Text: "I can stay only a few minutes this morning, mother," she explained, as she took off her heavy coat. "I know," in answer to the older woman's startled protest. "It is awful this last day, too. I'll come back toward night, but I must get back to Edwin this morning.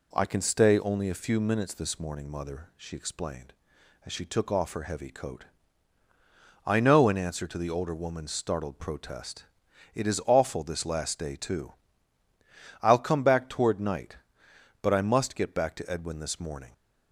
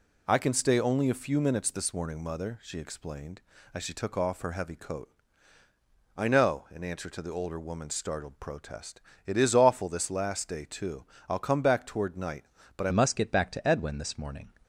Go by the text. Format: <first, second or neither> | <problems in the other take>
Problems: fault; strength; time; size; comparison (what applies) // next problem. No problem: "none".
first | changes voice at "must"; from 12.8 s on; 1.7 s long